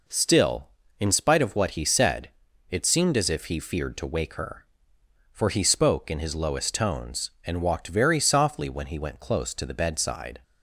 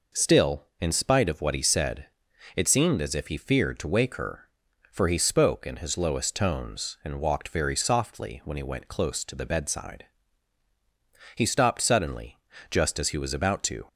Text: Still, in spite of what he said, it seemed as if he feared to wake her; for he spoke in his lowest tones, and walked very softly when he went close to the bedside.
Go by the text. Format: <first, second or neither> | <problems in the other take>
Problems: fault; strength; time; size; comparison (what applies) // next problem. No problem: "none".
first | goes on to say "He stopped suddenly just as he was about to"; strong; from 11.3 s on; 2.5 s long